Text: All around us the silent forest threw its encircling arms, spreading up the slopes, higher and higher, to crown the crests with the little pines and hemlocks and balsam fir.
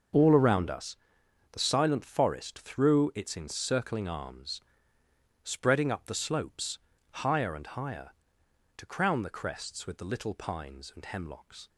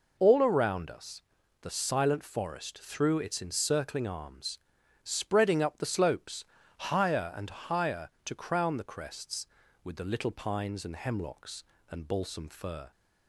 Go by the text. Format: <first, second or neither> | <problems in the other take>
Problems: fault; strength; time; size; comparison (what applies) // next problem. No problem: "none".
second | starts louder than the rest; until 1.6 s; 6 dB // pauses between "us" and "the"; noticeable; at 0.9 s; 0.54 s long; also in the second // stops before "and balsam fir"; at 11.6 s